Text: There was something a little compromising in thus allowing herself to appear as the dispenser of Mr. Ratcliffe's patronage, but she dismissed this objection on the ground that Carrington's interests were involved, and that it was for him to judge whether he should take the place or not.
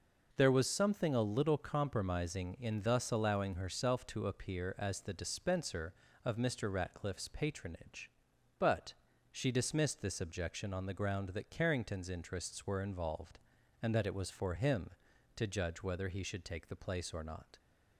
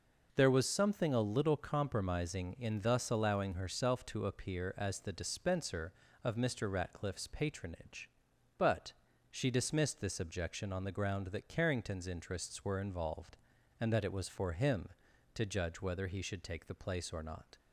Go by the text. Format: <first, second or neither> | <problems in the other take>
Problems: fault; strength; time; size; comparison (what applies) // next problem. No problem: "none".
neither | pauses between "but" and "she"; slight; the same in both